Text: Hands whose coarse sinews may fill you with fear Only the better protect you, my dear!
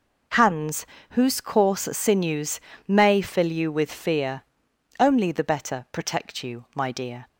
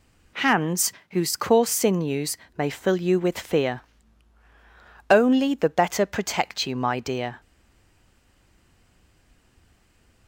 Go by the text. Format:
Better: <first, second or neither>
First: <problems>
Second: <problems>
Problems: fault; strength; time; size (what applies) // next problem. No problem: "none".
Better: first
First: pauses between "Hands" and "whose"; slight; at 0.8 s; 0.24 s long // pauses between "sinews" and "may"; slight; at 2.5 s; 0.26 s long // pauses between "fear" and "Only"; noticeable; at 4.4 s; 0.58 s long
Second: pauses between "Hands" and "whose"; slight; at 0.9 s; 0.20 s long // pauses between "sinews" and "may"; slight; at 2.3 s; 0.22 s long // pauses between "fear" and "Only"; strong; at 3.8 s; 1.2 s long // stays silent after the last word; strong; from 7.3 s on; 2.9 s long